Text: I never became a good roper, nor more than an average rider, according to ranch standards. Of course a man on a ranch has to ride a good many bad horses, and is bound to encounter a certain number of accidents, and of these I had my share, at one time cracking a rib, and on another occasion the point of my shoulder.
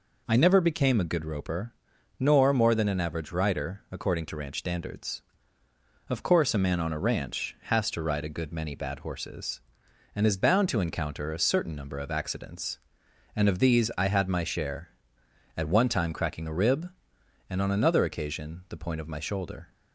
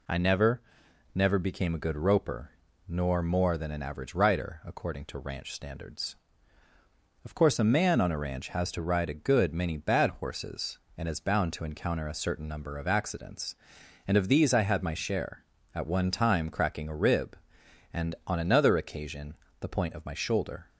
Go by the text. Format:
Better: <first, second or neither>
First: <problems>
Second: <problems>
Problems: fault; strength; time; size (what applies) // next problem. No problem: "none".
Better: first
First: none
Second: says "never" twice; at 1.1 s // pauses between "occasion" and "the"; slight; at 19.3 s; 0.26 s long